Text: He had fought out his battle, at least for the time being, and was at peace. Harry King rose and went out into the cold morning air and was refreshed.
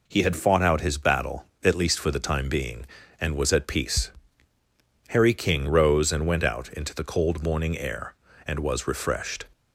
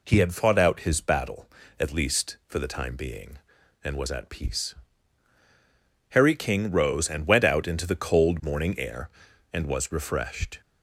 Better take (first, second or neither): neither